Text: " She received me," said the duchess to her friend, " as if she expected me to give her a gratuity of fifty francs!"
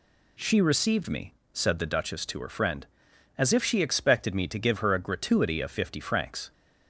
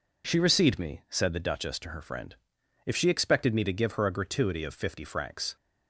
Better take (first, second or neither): first